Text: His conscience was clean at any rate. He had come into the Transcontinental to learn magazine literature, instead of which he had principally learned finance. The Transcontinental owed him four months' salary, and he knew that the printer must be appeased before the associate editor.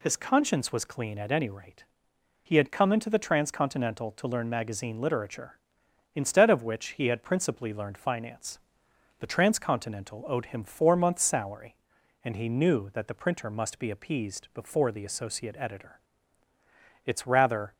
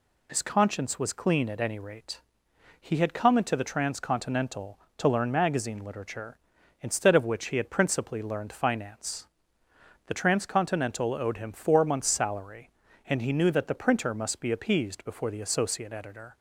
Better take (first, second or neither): second